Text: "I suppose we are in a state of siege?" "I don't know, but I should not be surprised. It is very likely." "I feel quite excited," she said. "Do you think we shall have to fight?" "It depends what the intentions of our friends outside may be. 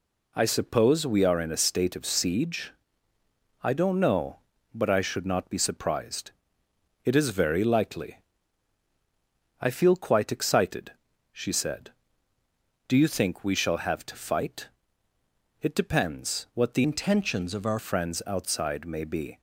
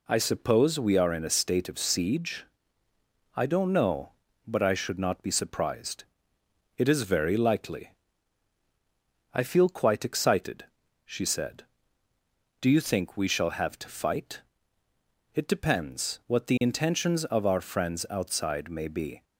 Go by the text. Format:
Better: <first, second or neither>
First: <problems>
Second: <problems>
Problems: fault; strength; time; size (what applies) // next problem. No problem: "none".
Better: second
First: changes voice from "intentions" to "our"; from 16.8 to 17.7 s; 0.9 s long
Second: none